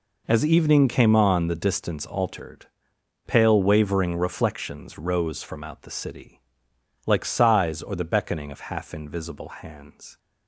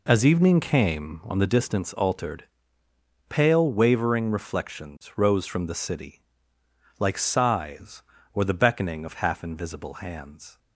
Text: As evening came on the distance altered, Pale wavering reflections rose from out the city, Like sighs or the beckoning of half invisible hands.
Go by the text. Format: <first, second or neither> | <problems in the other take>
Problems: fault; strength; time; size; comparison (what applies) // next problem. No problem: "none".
first | skips "out"; at 5.6 s